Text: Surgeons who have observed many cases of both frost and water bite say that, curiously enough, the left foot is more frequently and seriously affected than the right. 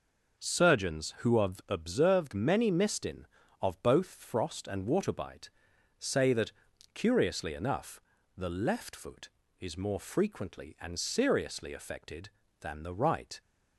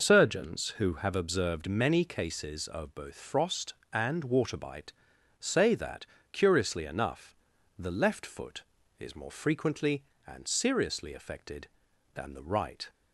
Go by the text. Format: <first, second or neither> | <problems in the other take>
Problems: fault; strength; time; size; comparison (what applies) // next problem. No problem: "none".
second | says "mistin" for "cases"; at 2.6 s // pauses between "bite" and "say"; noticeable; at 5.4 s; 0.48 s long; noticeable in the second